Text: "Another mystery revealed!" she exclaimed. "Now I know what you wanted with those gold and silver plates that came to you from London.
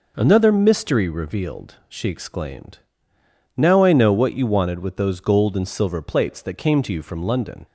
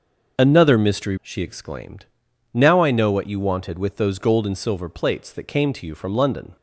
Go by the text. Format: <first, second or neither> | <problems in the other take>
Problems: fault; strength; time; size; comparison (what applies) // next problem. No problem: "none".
first | skips "revealed"; at 1.1 s